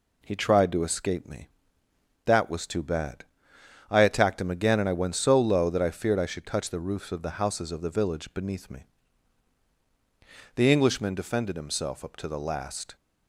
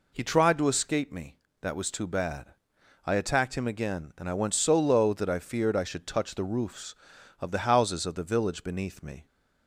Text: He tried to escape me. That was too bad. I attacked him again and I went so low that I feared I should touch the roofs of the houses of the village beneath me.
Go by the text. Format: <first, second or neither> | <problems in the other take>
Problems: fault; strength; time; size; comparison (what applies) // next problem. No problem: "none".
second | goes on to say "The Englishman defended himself up to the last"; strong; from 10.5 s on; 2.4 s long